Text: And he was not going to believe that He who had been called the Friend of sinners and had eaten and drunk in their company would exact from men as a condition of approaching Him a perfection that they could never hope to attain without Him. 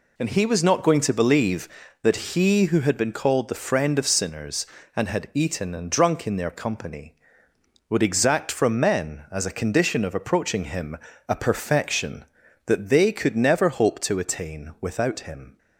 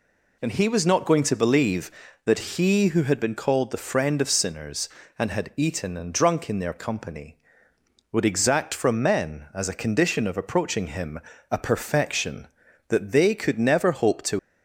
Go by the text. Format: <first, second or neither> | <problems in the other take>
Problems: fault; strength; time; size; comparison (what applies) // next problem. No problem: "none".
first | pauses between "Him" and "a"; slight; at 11.1 s; 0.32 s long; slight in the first // stops before "attain without Him"; at 14.3 s